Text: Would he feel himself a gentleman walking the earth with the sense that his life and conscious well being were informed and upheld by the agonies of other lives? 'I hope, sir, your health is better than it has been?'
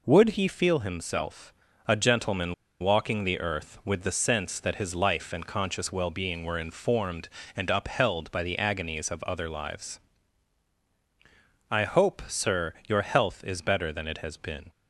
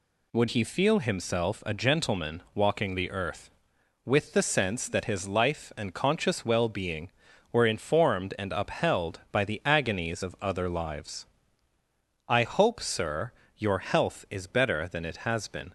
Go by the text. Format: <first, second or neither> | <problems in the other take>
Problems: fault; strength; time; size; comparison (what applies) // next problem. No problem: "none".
second | pauses between "himself" and "a"; slight; at 1.5 s; 0.32 s long // pauses between "gentleman" and "walking"; slight; at 2.5 s; 0.27 s long